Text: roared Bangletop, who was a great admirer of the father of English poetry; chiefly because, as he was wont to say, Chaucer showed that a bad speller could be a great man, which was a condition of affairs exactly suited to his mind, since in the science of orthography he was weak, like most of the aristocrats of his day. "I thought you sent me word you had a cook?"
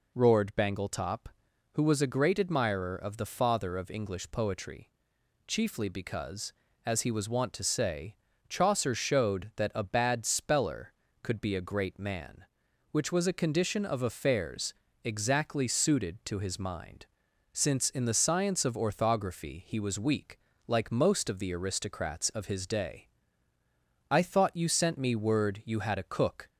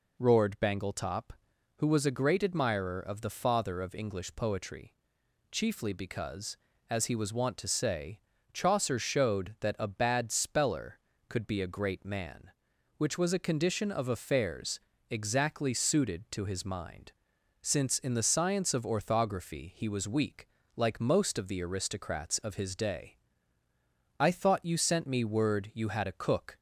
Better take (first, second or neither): neither